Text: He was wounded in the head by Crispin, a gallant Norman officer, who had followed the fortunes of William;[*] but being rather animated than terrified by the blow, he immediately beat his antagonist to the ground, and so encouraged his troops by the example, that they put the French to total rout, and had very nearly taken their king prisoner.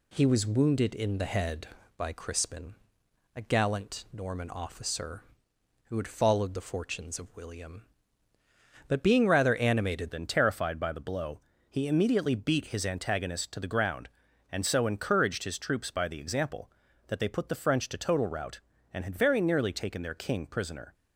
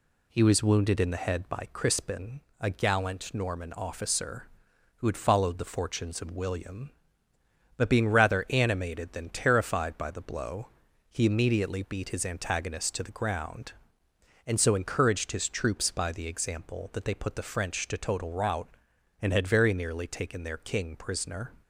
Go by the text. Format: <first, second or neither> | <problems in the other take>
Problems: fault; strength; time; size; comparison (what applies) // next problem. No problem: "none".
second | changes voice at "than"; from 10.1 s on; 10.8 s long